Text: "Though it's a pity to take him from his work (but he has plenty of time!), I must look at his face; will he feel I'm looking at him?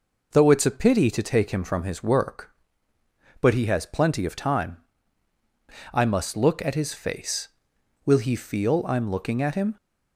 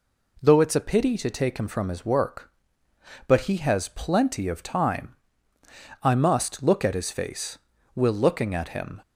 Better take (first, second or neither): first